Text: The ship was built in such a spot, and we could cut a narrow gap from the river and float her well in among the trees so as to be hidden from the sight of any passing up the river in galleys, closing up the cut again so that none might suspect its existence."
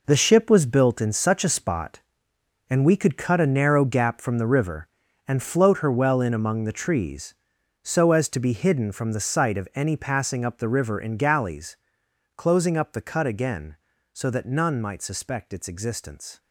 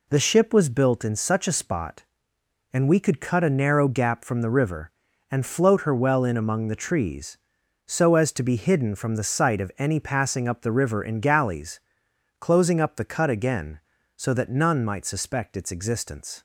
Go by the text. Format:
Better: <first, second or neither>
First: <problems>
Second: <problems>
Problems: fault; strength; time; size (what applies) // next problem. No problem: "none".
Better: second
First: gets quieter; strong; throughout; 10.5 dB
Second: none